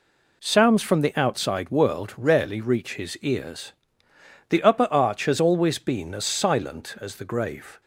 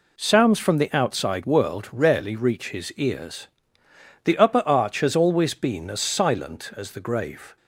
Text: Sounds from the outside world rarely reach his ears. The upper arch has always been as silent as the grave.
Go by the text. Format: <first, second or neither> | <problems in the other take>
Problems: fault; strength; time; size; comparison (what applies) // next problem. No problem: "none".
neither | none